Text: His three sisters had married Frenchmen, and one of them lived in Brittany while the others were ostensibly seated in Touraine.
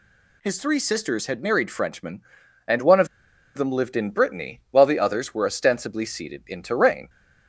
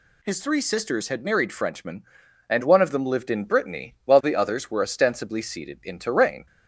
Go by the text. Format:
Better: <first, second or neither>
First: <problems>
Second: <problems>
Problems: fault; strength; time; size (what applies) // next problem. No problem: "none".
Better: second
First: pauses between "of" and "them"; noticeable; at 3.0 s; 0.49 s long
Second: none